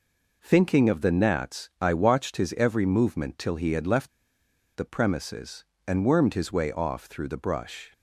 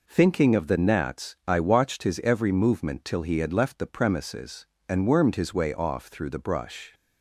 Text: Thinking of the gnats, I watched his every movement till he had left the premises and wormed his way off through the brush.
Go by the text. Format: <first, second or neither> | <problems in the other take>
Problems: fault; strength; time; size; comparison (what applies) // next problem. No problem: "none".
second | pauses between "left" and "the"; noticeable; at 4.0 s; 0.66 s long